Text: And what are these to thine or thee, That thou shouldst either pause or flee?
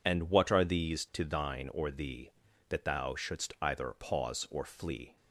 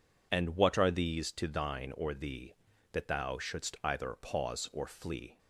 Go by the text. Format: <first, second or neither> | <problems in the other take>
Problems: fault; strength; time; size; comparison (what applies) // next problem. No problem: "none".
neither | none